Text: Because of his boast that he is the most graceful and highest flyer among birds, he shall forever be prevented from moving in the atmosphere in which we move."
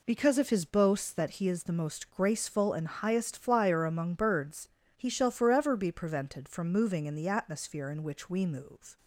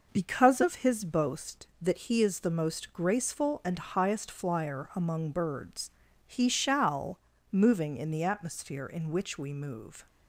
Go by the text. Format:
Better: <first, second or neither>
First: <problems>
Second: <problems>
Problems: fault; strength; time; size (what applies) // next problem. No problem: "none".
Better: first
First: none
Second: skips "forever be prevented from"; at 7.3 s